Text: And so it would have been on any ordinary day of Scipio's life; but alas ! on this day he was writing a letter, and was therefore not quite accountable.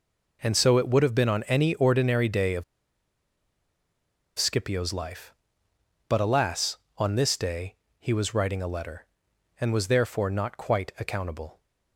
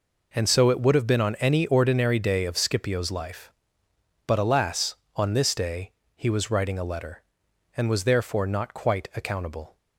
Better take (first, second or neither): second